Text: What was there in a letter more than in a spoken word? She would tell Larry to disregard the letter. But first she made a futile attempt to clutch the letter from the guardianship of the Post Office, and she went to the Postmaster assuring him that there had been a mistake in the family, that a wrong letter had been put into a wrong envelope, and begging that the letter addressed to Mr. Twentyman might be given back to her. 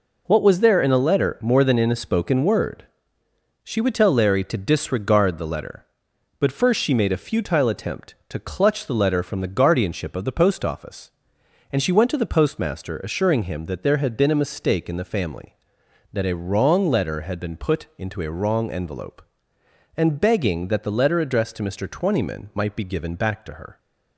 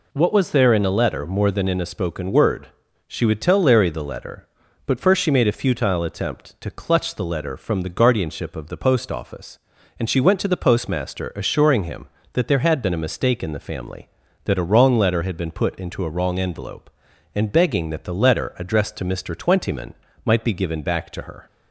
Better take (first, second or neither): first